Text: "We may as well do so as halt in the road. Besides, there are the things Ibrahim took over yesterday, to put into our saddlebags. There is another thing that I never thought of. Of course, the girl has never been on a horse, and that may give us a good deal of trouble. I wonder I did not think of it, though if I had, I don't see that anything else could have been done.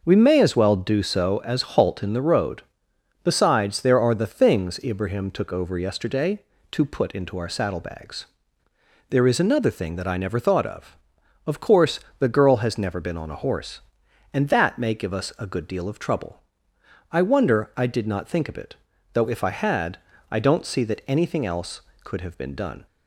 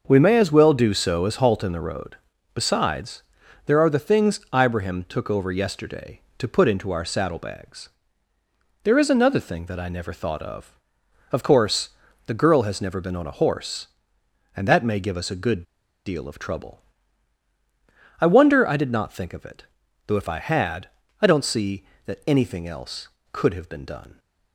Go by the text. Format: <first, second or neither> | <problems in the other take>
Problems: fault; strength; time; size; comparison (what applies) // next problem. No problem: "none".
first | starts louder than the rest; until 1.0 s; 6 dB // pauses between "good" and "deal"; at 15.6 s; 0.42 s long